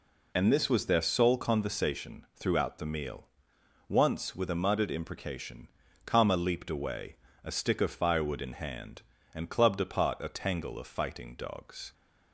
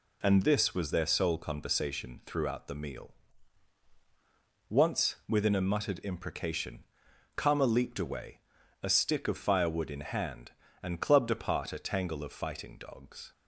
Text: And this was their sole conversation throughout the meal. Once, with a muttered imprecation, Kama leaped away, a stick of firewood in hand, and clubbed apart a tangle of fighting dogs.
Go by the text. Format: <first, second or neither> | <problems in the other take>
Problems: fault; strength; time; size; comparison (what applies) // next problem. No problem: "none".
first | says "within" for "with"; at 5.2 s